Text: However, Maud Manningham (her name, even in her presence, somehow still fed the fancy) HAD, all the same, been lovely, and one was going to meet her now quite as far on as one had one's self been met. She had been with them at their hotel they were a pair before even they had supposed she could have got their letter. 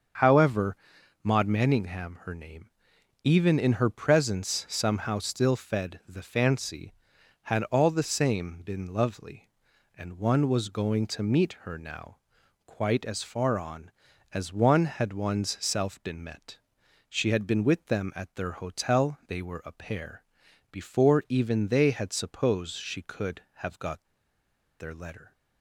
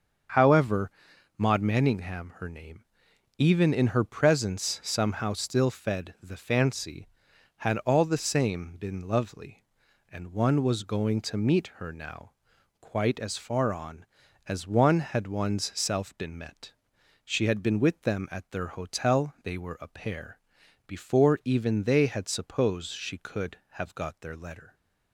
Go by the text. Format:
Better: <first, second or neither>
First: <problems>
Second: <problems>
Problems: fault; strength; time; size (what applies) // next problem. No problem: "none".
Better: second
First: starts louder than the rest; until 1.6 s; 7 dB // pauses between "now" and "quite"; noticeable; at 12.1 s; 0.48 s long // pauses between "pair" and "before"; noticeable; at 20.2 s; 0.50 s long // pauses between "got" and "their"; noticeable; at 24.0 s; 0.77 s long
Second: starts louder than the rest; until 1.8 s; 7 dB // pauses between "now" and "quite"; noticeable; at 12.3 s; 0.48 s long // pauses between "pair" and "before"; noticeable; at 20.3 s; 0.50 s long